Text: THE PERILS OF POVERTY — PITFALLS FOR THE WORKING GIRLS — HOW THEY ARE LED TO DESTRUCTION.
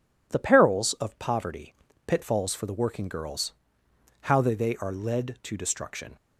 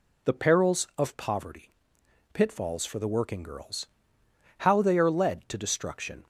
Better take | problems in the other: second | says "THEY" twice; at 4.5 s

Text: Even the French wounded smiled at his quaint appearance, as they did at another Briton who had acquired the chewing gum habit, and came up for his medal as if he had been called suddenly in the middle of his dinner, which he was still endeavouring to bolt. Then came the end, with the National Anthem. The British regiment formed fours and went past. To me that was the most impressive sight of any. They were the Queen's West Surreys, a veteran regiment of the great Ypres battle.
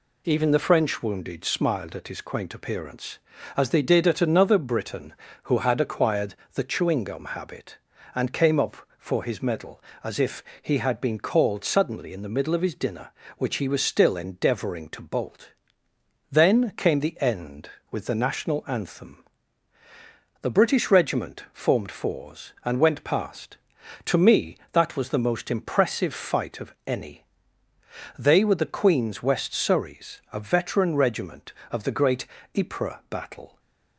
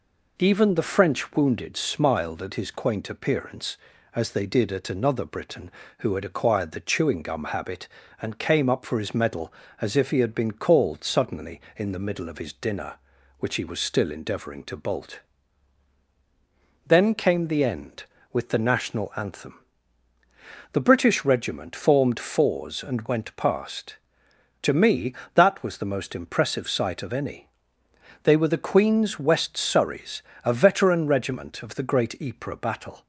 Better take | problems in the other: second | pauses between "acquired" and "the"; slight; at 6.3 s; 0.18 s long // pauses between "if" and "he"; slight; at 10.4 s; 0.18 s long // says "fight" for "sight"; at 26.1 s // pauses between "great" and "Ypres"; slight; at 32.2 s; 0.32 s long // stays silent after the last word; slight; from 33.4 s on; 0.5 s long

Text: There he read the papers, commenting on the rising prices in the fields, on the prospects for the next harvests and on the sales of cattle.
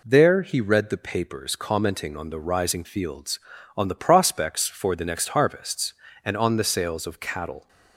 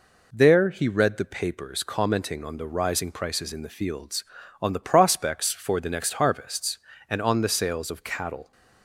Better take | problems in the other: second | skips "prices in the"; at 2.8 s

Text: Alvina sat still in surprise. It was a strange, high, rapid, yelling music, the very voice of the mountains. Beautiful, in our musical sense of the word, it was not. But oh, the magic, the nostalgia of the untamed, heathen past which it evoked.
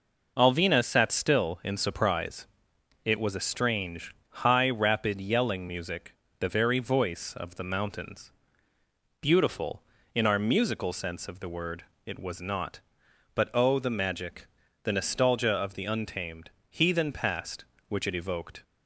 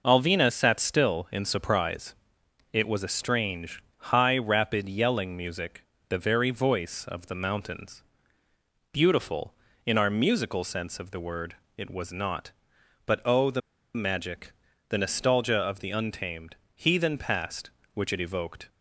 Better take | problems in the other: first | pauses between "the" and "magic"; slight; at 13.5 s; 0.34 s long

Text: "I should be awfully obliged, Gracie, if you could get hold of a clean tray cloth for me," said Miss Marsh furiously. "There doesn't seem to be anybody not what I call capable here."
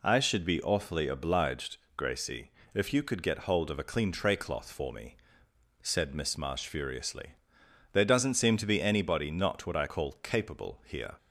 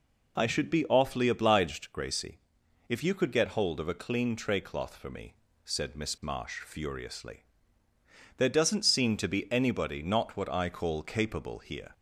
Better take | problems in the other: neither | none

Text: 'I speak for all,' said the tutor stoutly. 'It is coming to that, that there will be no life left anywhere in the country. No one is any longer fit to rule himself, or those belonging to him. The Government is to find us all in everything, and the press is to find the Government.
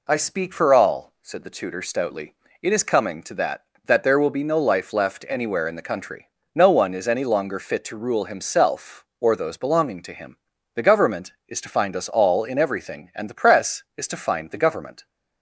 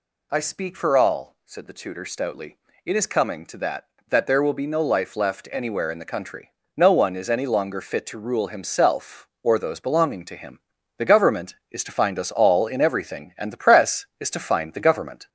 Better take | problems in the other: first | gets louder; throughout; 3.5 dB

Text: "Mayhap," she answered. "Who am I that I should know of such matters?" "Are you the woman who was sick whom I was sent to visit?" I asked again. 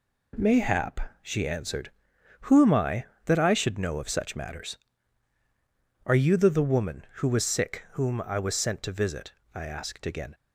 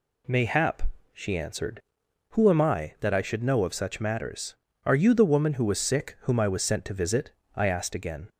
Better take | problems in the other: second | says "the" twice; at 6.5 s

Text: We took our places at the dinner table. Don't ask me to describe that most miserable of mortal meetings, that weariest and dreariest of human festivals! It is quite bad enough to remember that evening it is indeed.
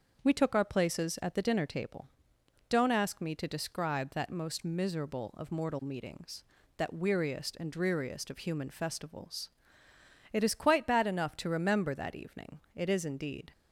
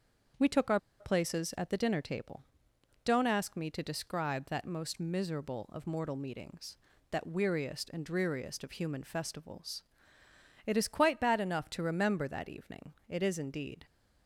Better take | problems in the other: first | starts louder than the rest; until 1.6 s; 6.5 dB; also in the first // pauses between "our" and "places"; slight; at 0.7 s; 0.20 s long // pauses between "evening" and "it"; slight; at 12.9 s; 0.16 s long; slight in the first

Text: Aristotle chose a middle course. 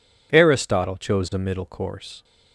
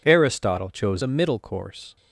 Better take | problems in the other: first | changes voice from "a" to "middle"; from 1.0 to 1.3 s; 0.3 s long

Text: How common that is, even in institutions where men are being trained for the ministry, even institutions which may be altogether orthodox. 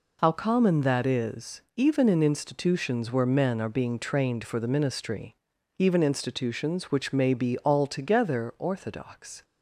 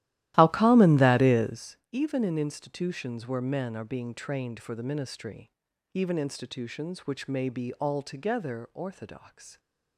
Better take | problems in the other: first | starts louder than the rest; strong; until 1.8 s; 14.5 dB

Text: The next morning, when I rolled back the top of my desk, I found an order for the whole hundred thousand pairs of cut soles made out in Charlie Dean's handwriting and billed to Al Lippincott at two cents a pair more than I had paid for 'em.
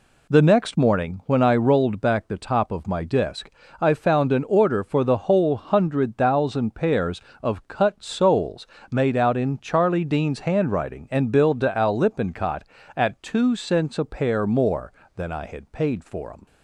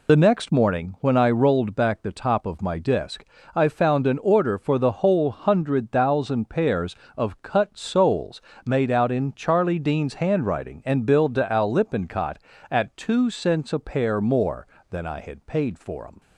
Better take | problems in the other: first | loses the start of "The"; at 0.0 s; 55 ms // pauses between "soles" and "made"; slight; at 8.3 s; 0.24 s long; slight in the first

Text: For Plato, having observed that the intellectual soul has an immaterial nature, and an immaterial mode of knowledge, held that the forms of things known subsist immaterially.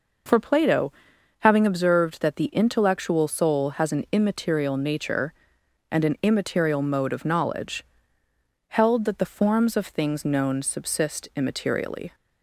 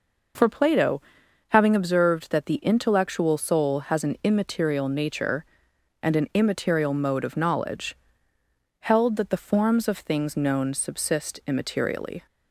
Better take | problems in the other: neither | none

